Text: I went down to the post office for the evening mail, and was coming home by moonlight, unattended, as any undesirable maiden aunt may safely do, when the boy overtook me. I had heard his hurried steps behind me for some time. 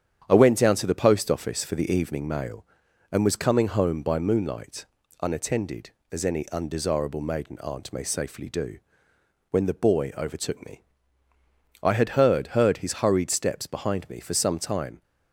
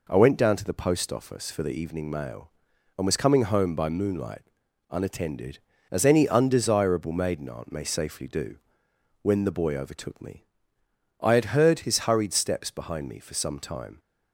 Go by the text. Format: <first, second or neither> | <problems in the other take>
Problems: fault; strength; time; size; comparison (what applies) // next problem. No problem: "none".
second | starts louder than the rest; strong; until 1.2 s; 8.5 dB // says "heard" twice; at 12.4 s